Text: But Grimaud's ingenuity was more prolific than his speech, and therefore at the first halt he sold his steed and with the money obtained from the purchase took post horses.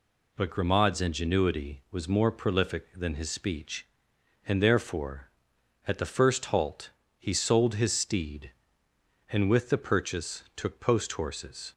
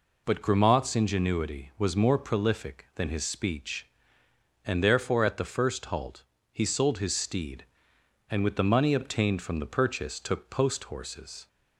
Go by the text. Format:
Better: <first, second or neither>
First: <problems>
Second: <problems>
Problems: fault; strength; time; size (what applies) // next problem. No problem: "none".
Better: second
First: pauses between "halt" and "he"; slight; at 6.8 s; 0.30 s long // skips "money obtained from the"; at 9.7 s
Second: pauses between "halt" and "he"; slight; at 6.2 s; 0.30 s long